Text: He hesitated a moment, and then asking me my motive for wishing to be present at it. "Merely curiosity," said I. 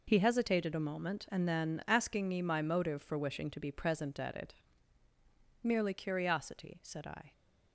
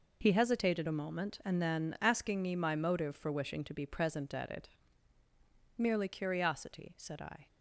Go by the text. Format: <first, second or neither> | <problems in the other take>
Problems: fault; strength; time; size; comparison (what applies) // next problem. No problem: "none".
neither | none